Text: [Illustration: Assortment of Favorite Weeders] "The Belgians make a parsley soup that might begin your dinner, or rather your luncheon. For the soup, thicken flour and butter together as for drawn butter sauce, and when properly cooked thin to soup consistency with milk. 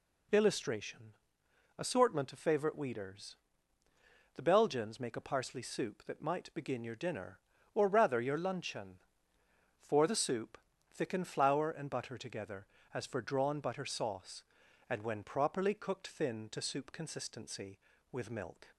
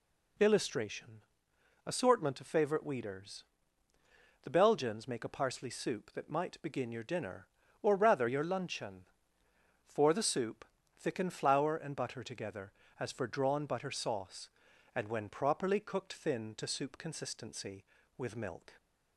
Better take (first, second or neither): neither